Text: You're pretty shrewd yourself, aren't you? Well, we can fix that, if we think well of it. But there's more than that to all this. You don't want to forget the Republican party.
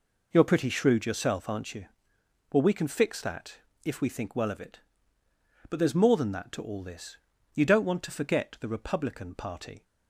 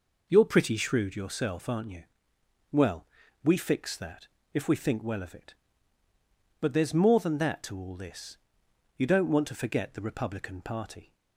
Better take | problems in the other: first | skips "can"; at 3.5 s

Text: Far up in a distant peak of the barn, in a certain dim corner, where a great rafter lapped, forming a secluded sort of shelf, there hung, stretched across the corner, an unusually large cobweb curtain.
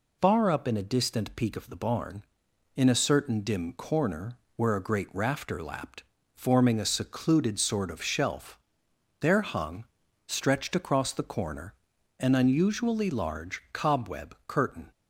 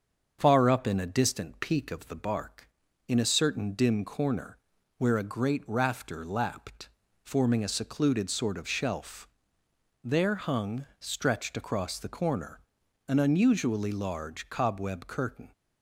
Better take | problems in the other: first | starts louder than the rest; until 1.4 s; 6.5 dB // says "bark" for "barn"; at 2.1 s

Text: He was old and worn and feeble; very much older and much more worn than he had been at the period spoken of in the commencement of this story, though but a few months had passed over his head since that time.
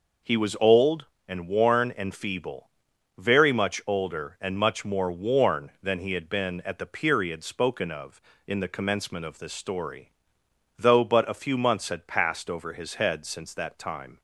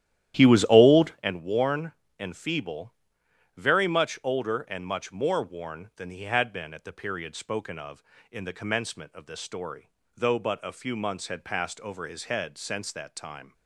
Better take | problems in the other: first | starts louder than the rest; strong; until 1.3 s; 12 dB

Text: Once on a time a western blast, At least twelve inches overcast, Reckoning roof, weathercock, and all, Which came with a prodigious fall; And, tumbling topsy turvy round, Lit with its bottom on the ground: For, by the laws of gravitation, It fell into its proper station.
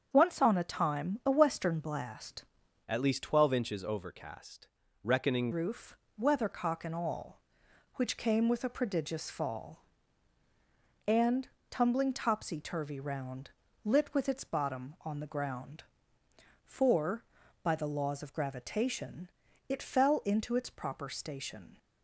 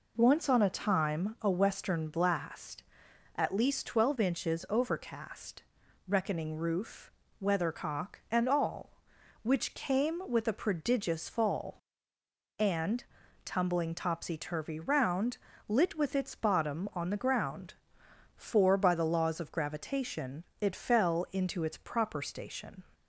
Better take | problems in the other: second | starts louder than the rest; strong; until 1.1 s; 7.5 dB // changes voice from "At" to "Reckoning"; from 2.8 to 5.5 s; 2.7 s long

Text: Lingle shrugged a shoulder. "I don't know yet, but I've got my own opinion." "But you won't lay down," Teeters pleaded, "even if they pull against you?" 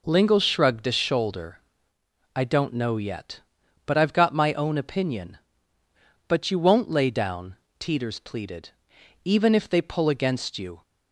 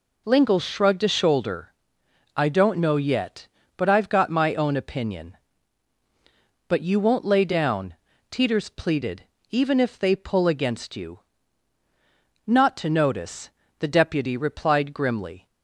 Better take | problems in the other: first | goes on to say "Not to notice the deputy replied grimly"; strong; from 12.4 s on; 3.0 s long

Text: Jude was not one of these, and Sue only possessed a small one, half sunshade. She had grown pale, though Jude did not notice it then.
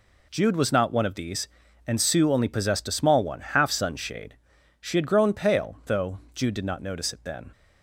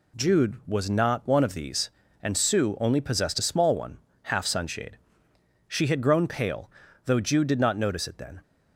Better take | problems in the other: neither | none

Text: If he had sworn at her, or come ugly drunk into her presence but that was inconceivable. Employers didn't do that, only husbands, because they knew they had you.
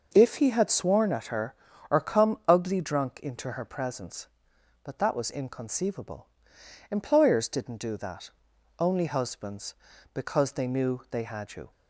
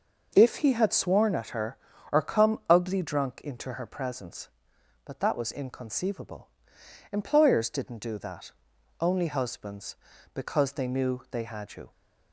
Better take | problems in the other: neither | none

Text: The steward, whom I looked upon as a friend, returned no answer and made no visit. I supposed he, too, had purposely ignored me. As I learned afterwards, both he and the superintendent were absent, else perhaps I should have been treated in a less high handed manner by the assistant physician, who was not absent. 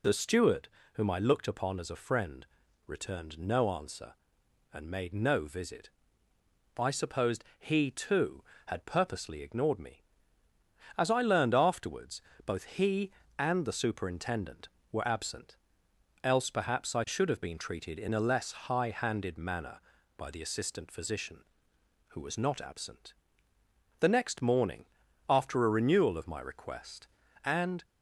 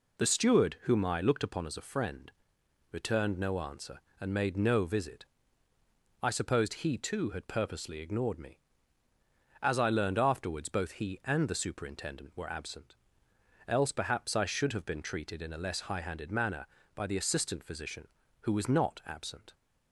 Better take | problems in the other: second | goes on to say "The next morning after a renewal of my request and"; strong; from 23.9 s on; 3.8 s long

